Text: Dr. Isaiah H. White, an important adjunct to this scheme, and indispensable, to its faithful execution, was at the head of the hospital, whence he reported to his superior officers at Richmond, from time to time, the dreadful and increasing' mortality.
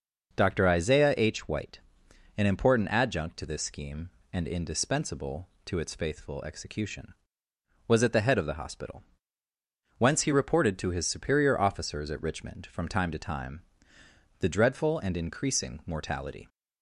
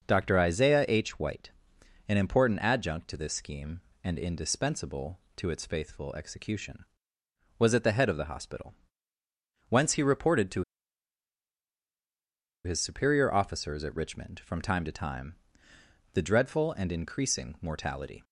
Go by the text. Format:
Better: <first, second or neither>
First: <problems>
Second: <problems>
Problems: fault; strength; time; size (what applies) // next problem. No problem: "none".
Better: first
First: none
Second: pauses between "to" and "his"; strong; at 10.6 s; 2.0 s long